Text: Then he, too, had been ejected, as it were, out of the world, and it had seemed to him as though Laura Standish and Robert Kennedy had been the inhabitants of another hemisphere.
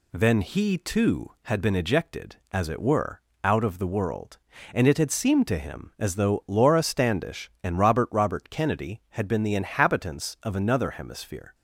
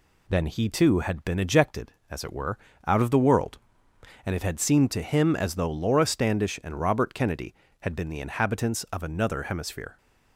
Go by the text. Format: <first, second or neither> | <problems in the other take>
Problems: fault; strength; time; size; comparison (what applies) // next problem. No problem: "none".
second | says "Robert" twice; at 8.1 s